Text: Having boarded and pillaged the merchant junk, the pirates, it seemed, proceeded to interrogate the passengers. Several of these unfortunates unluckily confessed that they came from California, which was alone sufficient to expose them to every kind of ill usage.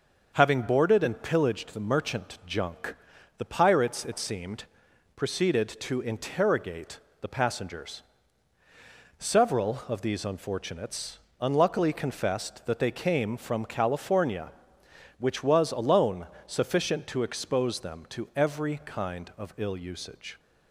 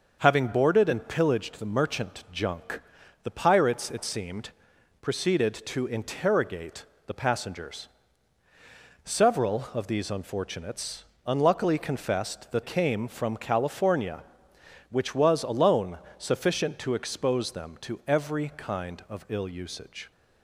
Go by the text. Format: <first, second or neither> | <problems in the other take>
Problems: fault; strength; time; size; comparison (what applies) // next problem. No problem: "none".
first | pauses between "interrogate" and "the"; slight; at 6.8 s; 0.22 s long; slight in the first // pauses between "unfortunates" and "unluckily"; slight; at 11.0 s; 0.20 s long; slight in the first // skips "they"; at 12.6 s // pauses between "alone" and "sufficient"; slight; at 15.9 s; 0.22 s long; slight in the first